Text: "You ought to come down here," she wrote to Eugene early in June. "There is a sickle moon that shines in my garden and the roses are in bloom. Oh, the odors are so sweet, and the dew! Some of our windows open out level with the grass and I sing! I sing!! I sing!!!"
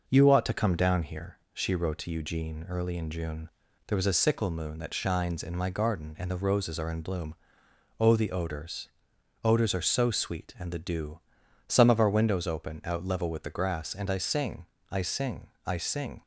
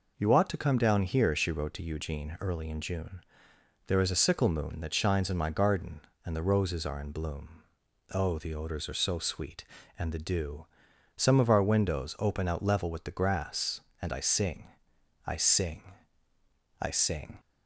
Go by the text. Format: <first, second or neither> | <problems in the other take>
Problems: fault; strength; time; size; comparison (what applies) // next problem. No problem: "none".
second | says "odors" twice; at 9.4 s